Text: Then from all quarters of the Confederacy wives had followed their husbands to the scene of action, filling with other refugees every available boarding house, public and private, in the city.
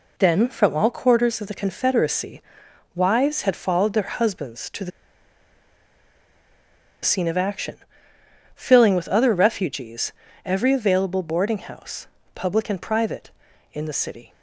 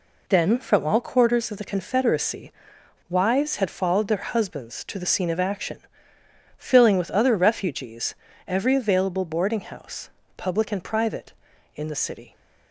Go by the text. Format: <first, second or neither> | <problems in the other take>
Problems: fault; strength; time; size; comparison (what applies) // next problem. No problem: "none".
second | pauses between "Confederacy" and "wives"; noticeable; at 2.4 s; 0.54 s long; noticeable in the second // pauses between "the" and "scene"; strong; at 4.9 s; 2.1 s long // pauses between "refugees" and "every"; slight; at 10.1 s; 0.34 s long; slight in the second